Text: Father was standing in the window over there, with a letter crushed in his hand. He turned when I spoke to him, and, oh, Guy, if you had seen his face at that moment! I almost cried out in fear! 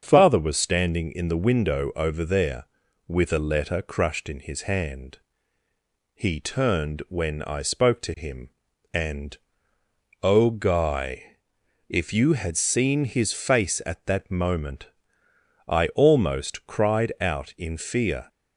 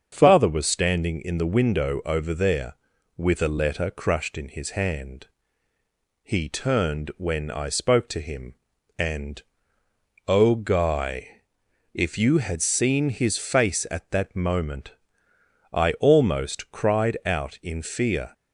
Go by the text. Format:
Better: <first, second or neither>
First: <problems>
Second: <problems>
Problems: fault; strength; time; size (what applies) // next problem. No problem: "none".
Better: neither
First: starts louder than the rest; until 1.0 s; 6.5 dB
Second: starts louder than the rest; until 1.1 s; 6.5 dB